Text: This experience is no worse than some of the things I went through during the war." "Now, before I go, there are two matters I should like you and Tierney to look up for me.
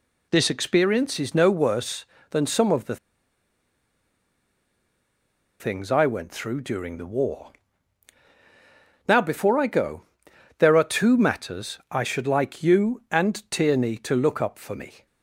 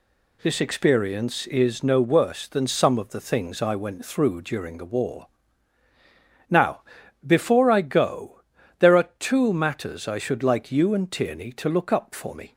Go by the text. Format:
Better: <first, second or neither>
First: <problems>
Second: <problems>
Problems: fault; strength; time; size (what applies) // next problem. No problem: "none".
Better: second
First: pauses between "the" and "things"; strong; at 2.9 s; 2.6 s long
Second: none